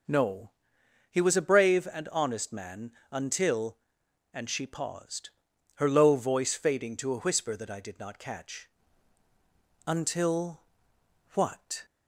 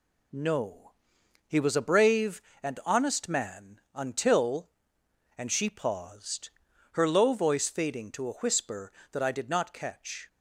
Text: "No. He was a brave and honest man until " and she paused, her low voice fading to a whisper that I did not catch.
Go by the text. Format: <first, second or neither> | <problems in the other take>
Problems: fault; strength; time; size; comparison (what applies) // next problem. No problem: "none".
second | pauses between "man" and "until"; slight; at 2.9 s; 0.18 s long; slight in the second // goes on to say "Until what"; strong; from 9.8 s on; 1.9 s long